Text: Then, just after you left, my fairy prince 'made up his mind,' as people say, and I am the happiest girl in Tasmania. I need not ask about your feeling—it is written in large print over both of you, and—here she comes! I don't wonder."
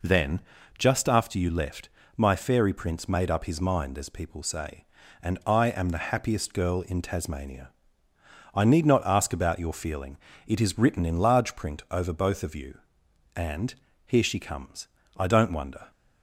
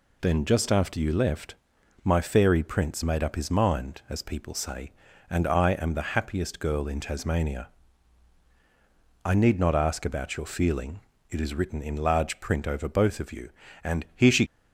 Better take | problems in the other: first | stops before "comes I don't wonder"; at 14.4 s

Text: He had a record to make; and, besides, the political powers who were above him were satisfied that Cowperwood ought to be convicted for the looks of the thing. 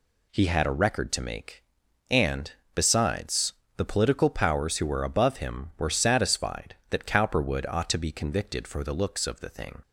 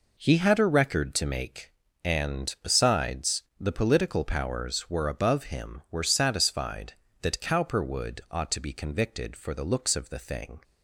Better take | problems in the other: first | skips "who"; at 4.8 s

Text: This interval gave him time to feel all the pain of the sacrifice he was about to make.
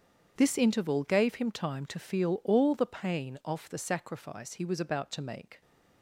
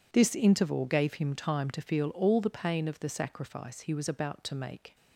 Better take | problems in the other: second | starts louder than the rest; strong; until 1.3 s; 7.5 dB // says "off" for "of"; at 3.4 s

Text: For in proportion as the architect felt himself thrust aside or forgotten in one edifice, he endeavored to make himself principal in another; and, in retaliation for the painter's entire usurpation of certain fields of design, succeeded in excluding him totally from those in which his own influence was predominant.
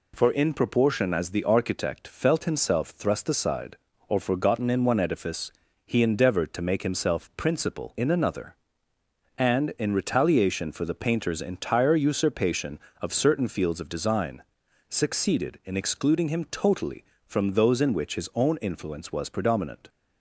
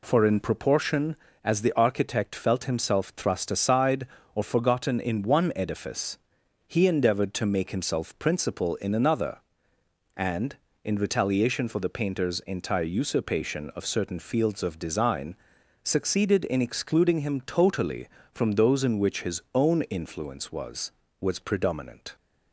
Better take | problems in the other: first | says "was" twice; at 21.2 s

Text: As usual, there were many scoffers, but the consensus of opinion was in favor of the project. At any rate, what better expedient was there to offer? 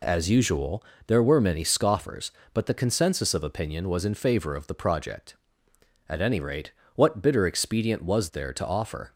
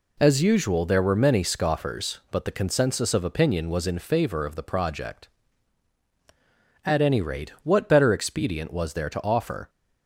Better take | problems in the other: second | says "bitter" for "better"; at 7.2 s

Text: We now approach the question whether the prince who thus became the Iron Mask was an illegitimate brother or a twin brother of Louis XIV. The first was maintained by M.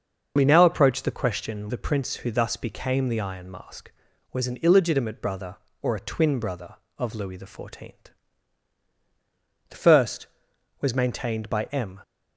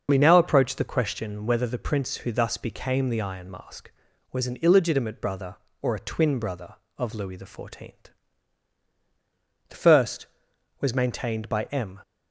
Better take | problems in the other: second | starts louder than the rest; until 1.3 s; 6 dB; also in the second // skips "whether"; at 1.7 s

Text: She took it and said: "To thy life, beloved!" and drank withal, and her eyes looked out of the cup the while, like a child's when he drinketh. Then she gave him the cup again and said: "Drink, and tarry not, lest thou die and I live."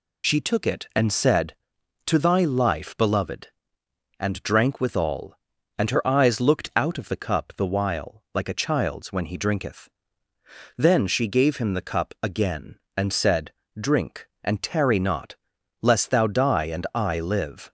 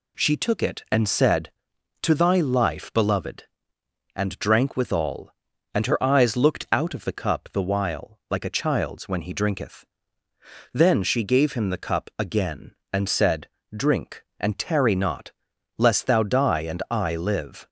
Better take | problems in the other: second | loses the start of "She"; at 0.2 s; 45 ms

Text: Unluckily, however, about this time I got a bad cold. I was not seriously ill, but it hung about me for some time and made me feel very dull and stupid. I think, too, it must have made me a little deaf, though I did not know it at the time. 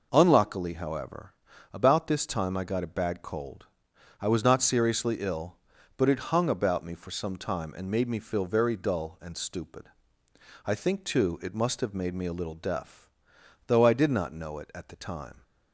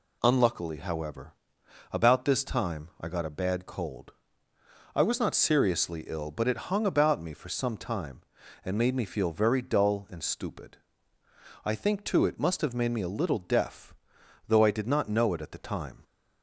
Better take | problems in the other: neither | none

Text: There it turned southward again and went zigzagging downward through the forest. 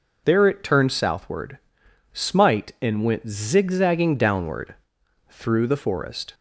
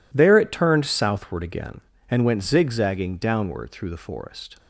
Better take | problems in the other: second | says "smite" for "again"; at 2.1 s // pauses between "downward" and "through"; noticeable; at 4.7 s; 0.54 s long

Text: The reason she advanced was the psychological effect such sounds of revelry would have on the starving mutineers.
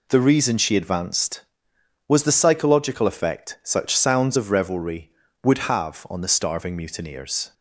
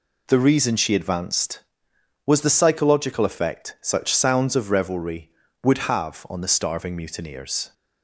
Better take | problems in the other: neither | none

